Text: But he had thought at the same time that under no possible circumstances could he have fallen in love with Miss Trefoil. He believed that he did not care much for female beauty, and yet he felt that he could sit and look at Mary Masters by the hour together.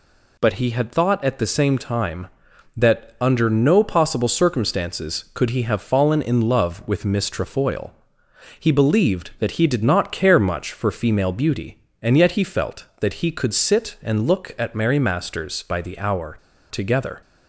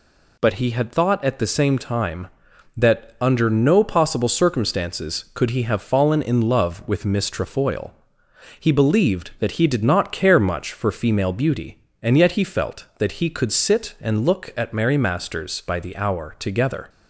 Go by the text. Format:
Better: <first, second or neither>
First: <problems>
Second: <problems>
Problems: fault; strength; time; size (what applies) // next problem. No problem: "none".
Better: second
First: pauses between "hour" and "together"; slight; at 16.3 s; 0.33 s long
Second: none